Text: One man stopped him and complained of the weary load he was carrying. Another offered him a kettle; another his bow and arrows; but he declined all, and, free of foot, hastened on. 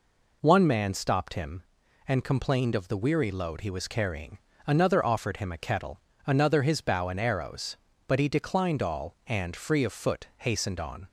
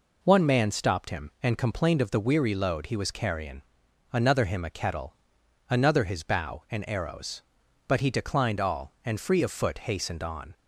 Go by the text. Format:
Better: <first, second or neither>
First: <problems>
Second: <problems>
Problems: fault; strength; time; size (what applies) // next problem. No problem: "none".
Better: first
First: none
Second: skips "offered"; at 4.4 s